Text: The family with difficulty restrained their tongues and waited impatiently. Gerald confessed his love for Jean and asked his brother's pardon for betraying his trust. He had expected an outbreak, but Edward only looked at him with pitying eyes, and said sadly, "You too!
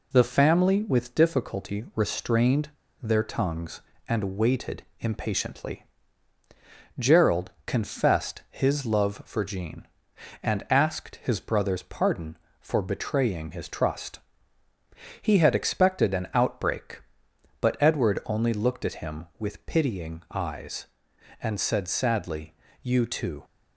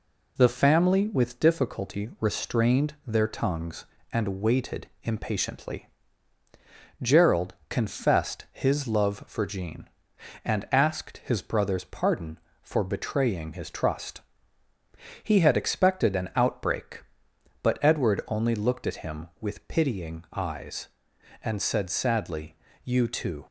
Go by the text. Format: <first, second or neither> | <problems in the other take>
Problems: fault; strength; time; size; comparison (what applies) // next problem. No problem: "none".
second | pauses between "restrained" and "their"; slight; at 2.7 s; 0.30 s long // pauses between "waited" and "impatiently"; slight; at 4.8 s; 0.16 s long